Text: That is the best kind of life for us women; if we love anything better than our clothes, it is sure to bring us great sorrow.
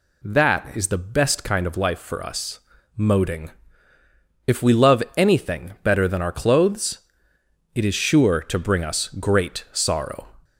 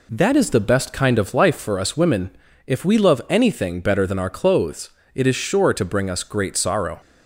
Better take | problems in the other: second | says "moding" for "women"; at 2.9 s

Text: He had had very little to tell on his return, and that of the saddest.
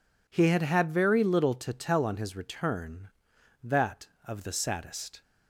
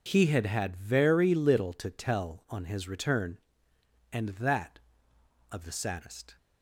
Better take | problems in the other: second | skips "and"; at 3.3 s

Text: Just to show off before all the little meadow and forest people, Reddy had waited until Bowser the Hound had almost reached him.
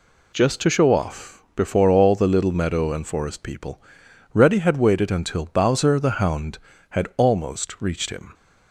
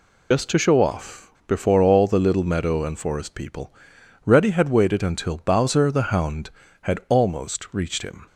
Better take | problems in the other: first | loses the start of "Just"; at 0.3 s; 80 ms

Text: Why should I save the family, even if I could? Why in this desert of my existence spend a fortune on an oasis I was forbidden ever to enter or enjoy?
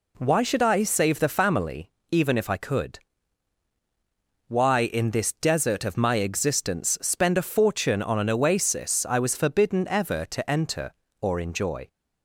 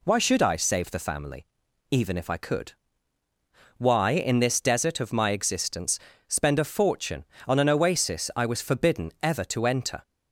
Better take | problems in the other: first | pauses between "existence" and "spend"; slight; at 5.9 s; 0.30 s long // stops before "or enjoy"; at 10.0 s

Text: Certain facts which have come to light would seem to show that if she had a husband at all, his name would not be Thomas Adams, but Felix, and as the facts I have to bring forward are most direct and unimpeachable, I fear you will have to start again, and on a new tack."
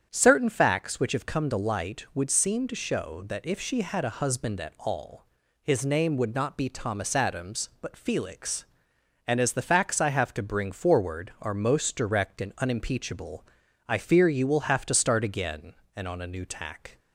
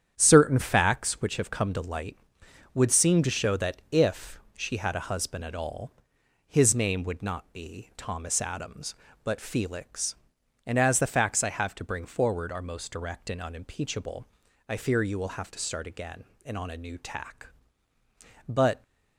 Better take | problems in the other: first | starts louder than the rest; strong; until 1.1 s; 9 dB; strong in the first // pauses between "if" and "she"; slight; at 4.3 s; 0.16 s long // goes on to say "But"; slight; from 18.4 s on; 0.34 s long

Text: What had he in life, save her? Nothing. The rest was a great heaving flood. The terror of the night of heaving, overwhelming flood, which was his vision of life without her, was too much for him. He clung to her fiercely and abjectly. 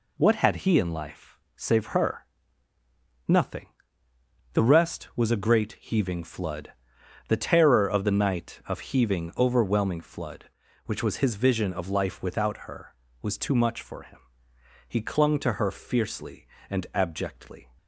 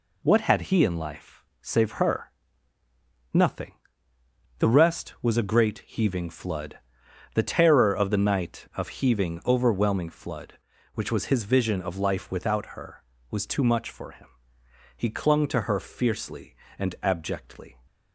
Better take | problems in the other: neither | none

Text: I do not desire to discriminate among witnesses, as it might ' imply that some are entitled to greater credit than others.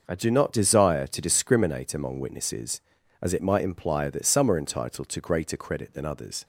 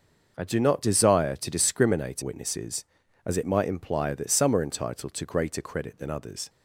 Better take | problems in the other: first | starts louder than the rest; noticeable; until 1.3 s; 6 dB // skips "among"; at 2.2 s

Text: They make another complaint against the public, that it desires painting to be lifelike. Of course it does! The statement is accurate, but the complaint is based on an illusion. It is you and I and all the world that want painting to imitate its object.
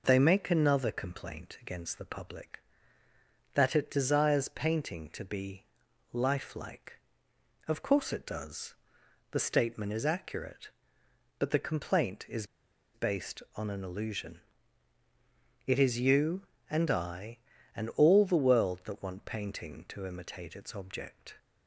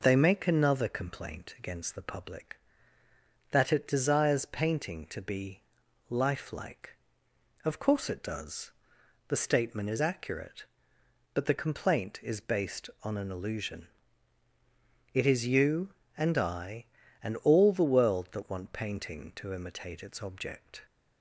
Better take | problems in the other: second | pauses between "be" and "lifelike"; noticeable; at 5.6 s; 0.48 s long; noticeable in the second // pauses between "is" and "based"; noticeable; at 12.4 s; 0.49 s long

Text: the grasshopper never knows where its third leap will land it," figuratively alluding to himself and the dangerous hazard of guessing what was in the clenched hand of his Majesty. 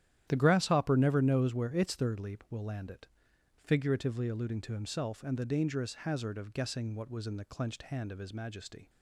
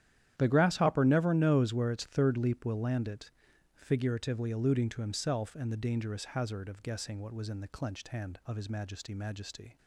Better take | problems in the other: first | starts louder than the rest; strong; until 1.3 s; 10.5 dB; strong in the first // says "Majesty" twice; at 9.1 s

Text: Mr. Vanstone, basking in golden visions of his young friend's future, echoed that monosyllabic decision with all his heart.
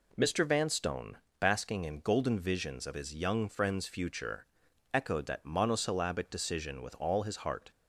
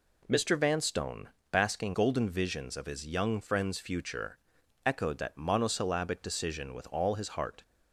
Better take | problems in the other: first | skips "in"; at 1.9 s

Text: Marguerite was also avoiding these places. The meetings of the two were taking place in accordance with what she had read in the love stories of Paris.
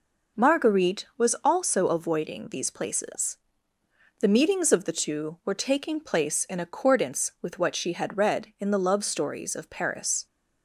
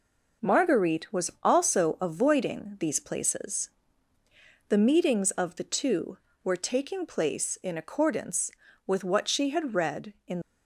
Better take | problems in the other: first | stops before "the love stories of Paris"; at 10.4 s

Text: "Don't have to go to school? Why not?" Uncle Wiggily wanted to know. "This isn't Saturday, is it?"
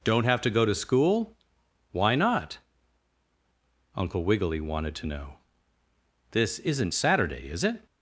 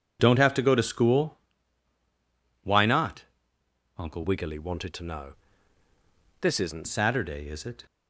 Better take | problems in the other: first | changes voice from "Wiggily" to "isn't"; from 4.2 to 6.8 s; 2.6 s long

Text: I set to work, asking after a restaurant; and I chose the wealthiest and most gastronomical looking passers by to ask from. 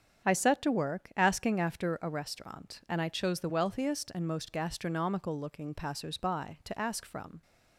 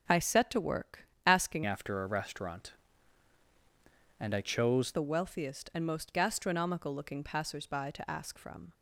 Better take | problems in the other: first | starts louder than the rest; until 1.2 s; 7 dB; strong in the first // changes voice from "after" to "chose"; from 1.6 to 4.9 s; 3.3 s long

